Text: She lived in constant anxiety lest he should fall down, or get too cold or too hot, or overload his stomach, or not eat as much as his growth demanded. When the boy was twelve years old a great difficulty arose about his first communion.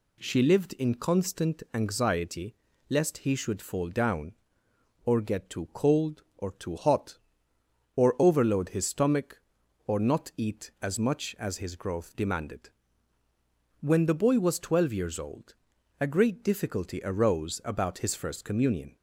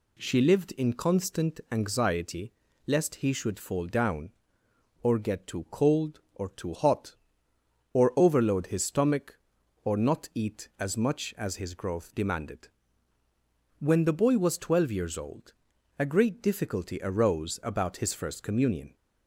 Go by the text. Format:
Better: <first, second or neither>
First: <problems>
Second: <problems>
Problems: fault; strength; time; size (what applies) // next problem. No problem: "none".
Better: neither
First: pauses between "anxiety" and "lest"; slight; at 2.5 s; 0.36 s long // pauses between "old" and "a"; noticeable; at 15.5 s; 0.46 s long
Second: pauses between "anxiety" and "lest"; slight; at 2.5 s; 0.36 s long // pauses between "old" and "a"; noticeable; at 15.5 s; 0.46 s long